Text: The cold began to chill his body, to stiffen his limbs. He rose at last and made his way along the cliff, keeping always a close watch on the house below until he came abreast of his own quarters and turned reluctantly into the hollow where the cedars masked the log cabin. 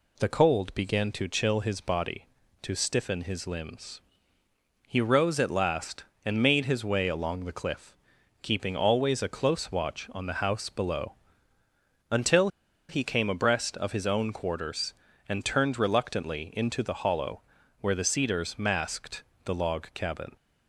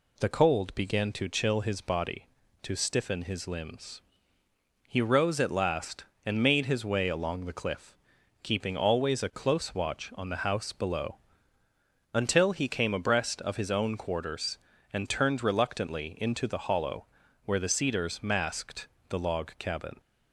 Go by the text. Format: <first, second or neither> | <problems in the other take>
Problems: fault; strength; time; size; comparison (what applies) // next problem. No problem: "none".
second | pauses between "below" and "until"; noticeable; at 11.1 s; 0.96 s long; noticeable in the second // pauses between "until" and "he"; at 12.4 s; 0.41 s long // pauses between "hollow" and "where"; at 17.3 s; 0.40 s long; also in the second // pauses between "masked" and "the"; slight; at 19.2 s; 0.22 s long; slight in the second